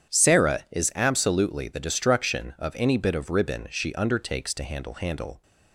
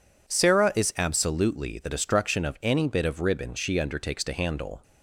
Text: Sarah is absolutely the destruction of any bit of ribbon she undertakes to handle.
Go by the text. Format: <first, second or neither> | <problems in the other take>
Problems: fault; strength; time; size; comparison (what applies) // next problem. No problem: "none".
second | starts louder than the rest; strong; until 1.2 s; 9 dB // says "handle" twice; at 4.9 s